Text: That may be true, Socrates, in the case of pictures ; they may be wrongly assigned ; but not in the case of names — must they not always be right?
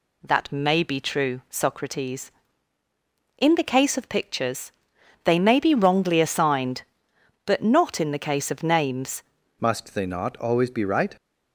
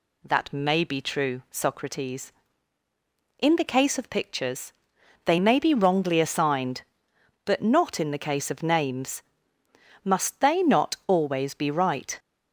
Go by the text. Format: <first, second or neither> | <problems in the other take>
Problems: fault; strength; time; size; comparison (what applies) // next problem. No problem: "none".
second | changes voice at "must"; from 9.5 s on; 1.6 s long